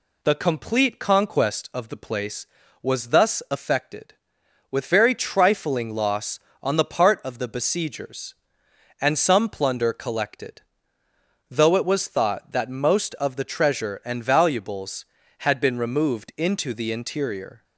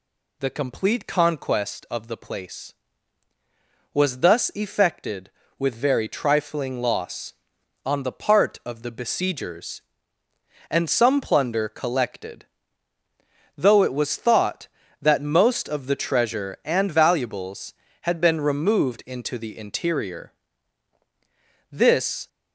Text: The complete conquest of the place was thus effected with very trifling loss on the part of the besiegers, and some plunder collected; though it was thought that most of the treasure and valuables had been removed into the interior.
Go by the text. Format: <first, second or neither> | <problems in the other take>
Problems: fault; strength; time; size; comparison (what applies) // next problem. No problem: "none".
first | goes on to say "This"; from 21.7 s on; 0.56 s long